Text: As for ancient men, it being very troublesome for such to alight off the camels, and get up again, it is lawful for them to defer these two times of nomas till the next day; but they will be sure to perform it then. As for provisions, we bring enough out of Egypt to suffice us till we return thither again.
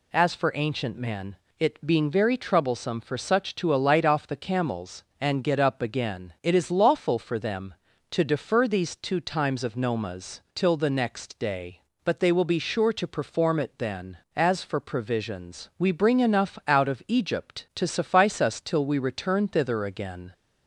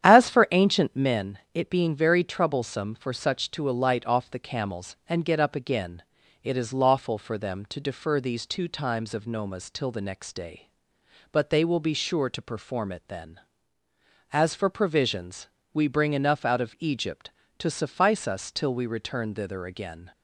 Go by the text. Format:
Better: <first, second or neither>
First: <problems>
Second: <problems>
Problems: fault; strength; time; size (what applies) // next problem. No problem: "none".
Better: first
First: none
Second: starts louder than the rest; strong; until 1.3 s; 9.5 dB